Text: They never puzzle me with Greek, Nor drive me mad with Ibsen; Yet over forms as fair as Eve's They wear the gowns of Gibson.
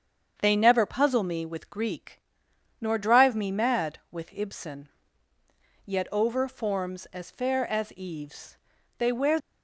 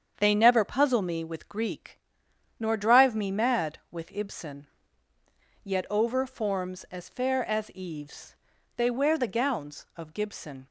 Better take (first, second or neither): second